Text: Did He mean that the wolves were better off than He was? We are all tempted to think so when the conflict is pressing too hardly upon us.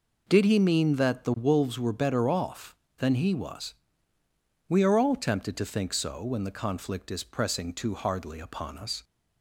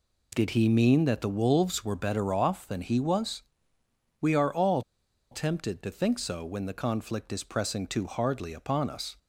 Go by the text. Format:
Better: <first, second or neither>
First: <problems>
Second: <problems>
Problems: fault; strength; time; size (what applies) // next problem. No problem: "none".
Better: first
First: none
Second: pauses between "all" and "tempted"; noticeable; at 4.8 s; 0.49 s long